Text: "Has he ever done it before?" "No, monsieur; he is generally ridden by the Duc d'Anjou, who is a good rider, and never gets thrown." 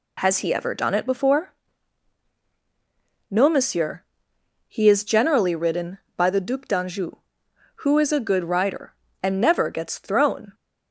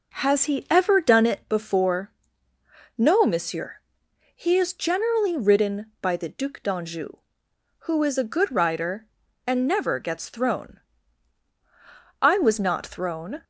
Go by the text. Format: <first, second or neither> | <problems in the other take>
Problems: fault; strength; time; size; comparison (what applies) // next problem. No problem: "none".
first | goes on to say "I was not thrown"; noticeable; from 12.2 s on; 1.2 s long